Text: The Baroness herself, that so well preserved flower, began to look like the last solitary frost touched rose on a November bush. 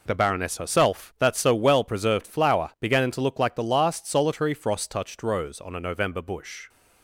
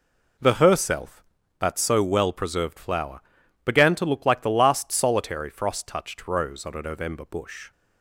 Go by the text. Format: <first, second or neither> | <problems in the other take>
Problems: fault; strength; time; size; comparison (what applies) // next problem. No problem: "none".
first | skips "Baroness"; at 0.5 s